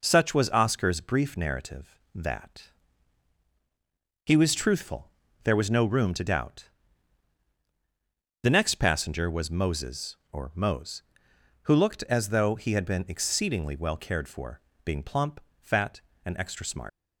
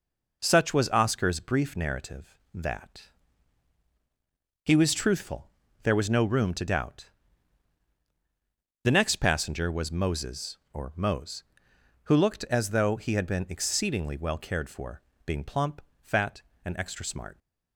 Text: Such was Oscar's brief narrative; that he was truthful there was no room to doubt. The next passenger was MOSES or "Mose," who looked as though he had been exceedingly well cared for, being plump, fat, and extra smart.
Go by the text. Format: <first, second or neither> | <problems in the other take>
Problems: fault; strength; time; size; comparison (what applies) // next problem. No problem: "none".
second | pauses between "that" and "he"; strong; at 2.7 s; 1.5 s long; strong in the second // pauses between "truthful" and "there"; slight; at 5.1 s; 0.34 s long; slight in the second // leaves "smart" unfinished; at 16.8 s; 90 ms